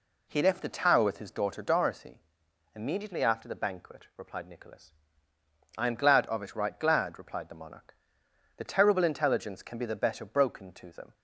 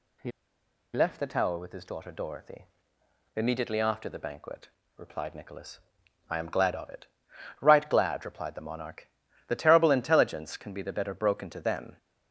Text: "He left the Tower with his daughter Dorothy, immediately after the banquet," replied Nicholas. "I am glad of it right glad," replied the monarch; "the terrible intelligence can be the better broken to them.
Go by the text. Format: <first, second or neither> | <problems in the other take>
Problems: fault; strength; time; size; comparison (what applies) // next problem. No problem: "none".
first | pauses between "He" and "left"; noticeable; at 0.3 s; 0.64 s long // pauses between "it" and "right"; noticeable; at 7.0 s; 0.56 s long